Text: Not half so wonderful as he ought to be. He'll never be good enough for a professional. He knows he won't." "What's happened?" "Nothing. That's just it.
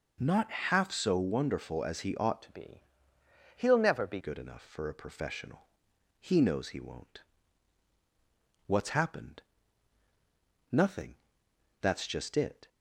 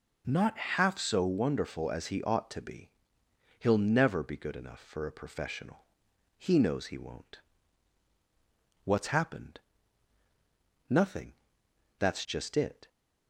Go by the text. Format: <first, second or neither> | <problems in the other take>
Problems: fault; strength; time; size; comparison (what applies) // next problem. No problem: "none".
second | changes voice from "to" to "be"; from 2.4 to 4.1 s; 1.7 s long